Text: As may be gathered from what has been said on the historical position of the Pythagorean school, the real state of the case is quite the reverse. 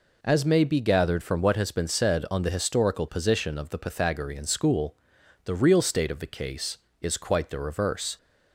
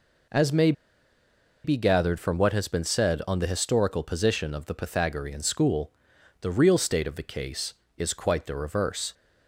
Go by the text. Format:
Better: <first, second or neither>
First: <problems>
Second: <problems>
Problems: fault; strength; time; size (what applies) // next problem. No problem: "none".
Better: first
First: none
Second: pauses between "may" and "be"; noticeable; at 0.7 s; 0.92 s long